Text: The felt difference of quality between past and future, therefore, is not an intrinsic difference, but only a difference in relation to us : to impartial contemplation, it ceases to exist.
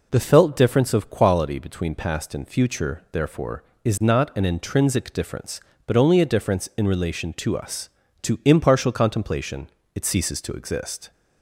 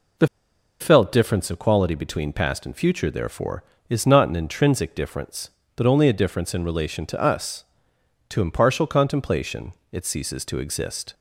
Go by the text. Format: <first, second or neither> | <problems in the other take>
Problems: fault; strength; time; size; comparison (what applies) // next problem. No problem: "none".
first | pauses between "The" and "felt"; noticeable; at 0.2 s; 0.53 s long